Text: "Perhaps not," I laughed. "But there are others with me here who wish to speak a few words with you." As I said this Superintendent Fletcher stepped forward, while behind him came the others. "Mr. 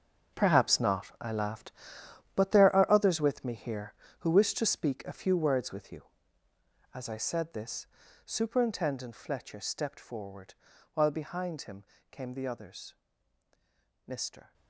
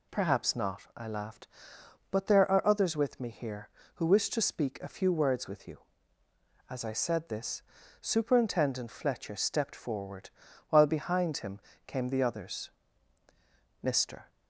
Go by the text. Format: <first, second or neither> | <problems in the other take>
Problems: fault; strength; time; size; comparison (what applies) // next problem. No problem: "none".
second | gets quieter; strong; throughout; 13.5 dB // pauses between "this" and "Superintendent"; at 7.8 s; 0.40 s long; also in the second // pauses between "him" and "came"; slight; at 11.8 s; 0.24 s long; slight in the second